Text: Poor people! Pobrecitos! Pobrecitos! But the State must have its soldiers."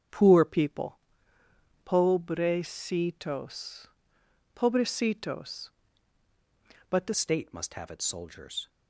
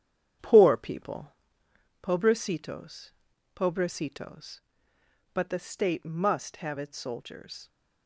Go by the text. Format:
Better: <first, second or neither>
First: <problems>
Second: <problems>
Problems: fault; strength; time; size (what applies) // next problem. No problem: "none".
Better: second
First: starts louder than the rest; strong; until 2.0 s; 8 dB // changes voice at "State"; from 7.1 s on; 1.5 s long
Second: starts louder than the rest; strong; until 2.1 s; 9 dB